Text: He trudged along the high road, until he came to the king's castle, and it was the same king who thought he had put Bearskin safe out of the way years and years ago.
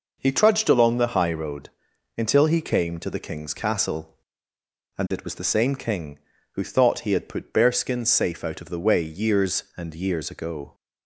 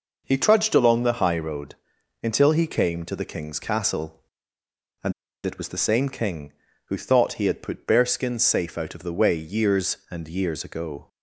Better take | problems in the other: first | pauses between "and" and "it"; slight; at 5.1 s; 0.33 s long

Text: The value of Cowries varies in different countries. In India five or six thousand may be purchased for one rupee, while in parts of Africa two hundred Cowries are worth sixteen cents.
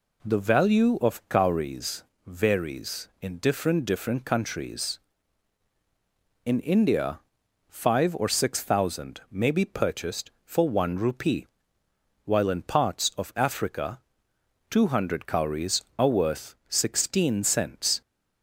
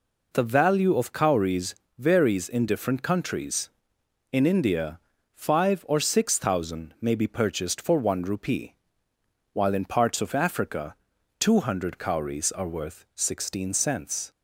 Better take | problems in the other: second | pauses between "Cowries" and "varies"; slight; at 2.0 s; 0.24 s long; slight in the second // says "different" twice; at 3.8 s // pauses between "India" and "five"; noticeable; at 7.1 s; 0.50 s long; slight in the second // pauses between "Africa" and "two"; noticeable; at 14.0 s; 0.68 s long; noticeable in the second

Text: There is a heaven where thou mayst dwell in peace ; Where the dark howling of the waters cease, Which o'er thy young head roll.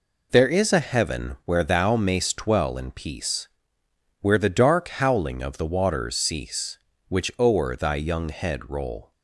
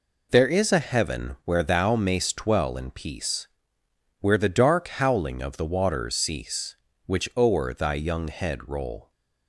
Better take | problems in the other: neither | none

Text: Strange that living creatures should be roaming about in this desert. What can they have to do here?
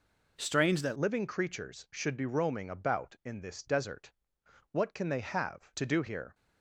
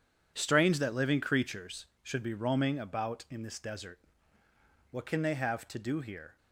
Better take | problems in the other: second | changes voice at "living"; from 0.9 s on; 5.4 s long

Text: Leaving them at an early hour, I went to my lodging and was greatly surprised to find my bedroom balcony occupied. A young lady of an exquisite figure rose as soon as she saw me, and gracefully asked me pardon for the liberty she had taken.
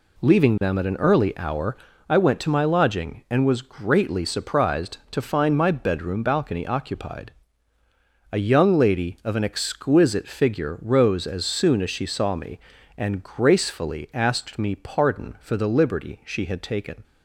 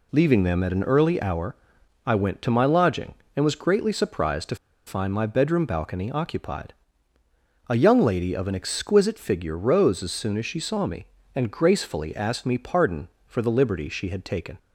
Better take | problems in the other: first | pauses between "to" and "find"; slight; at 4.5 s; 0.31 s long

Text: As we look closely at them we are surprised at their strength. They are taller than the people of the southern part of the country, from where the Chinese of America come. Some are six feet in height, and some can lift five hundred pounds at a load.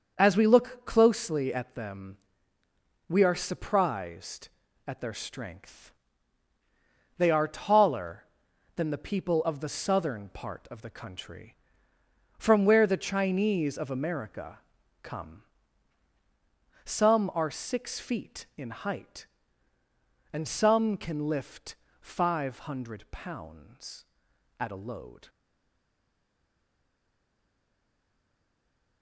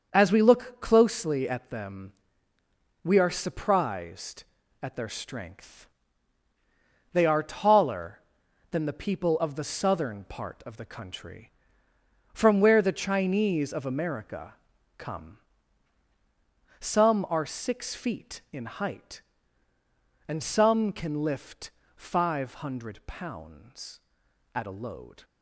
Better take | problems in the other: second | starts louder than the rest; until 1.1 s; 6.5 dB; also in the second // pauses between "them" and "we"; noticeable; at 2.1 s; 0.92 s long; noticeable in the second // pauses between "America" and "come"; at 14.5 s; 0.44 s long; also in the second // pauses between "lift" and "five"; slight; at 21.7 s; 0.26 s long; slight in the second // stays silent after the last word; strong; from 25.2 s on; 3.8 s long

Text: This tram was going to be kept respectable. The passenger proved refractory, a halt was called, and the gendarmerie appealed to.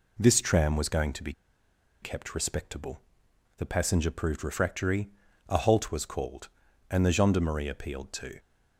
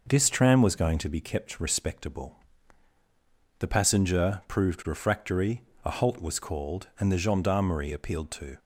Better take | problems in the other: second | pauses between "be" and "kept"; noticeable; at 1.3 s; 0.70 s long

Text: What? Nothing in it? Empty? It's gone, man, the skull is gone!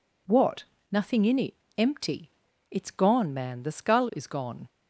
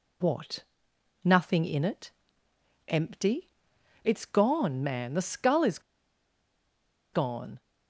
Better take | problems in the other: first | pauses between "is" and "gone"; strong; at 5.7 s; 1.3 s long

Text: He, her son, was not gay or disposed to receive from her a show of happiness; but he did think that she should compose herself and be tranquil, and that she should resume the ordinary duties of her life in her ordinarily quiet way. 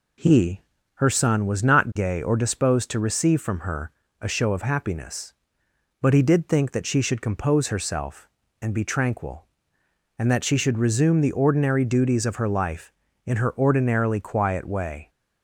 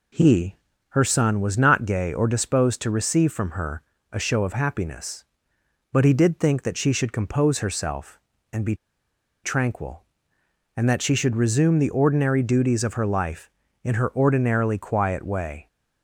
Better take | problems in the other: first | pauses between "her" and "a"; slight; at 3.8 s; 0.32 s long; slight in the first // pauses between "be" and "tranquil"; noticeable; at 8.7 s; 0.69 s long

